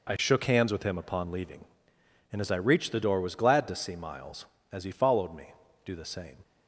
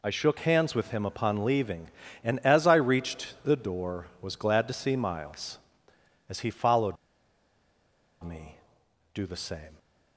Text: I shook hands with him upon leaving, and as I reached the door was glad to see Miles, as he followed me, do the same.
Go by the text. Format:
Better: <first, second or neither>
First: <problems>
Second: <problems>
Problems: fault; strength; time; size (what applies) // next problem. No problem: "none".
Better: first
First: none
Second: pauses between "followed" and "me"; strong; at 6.9 s; 1.2 s long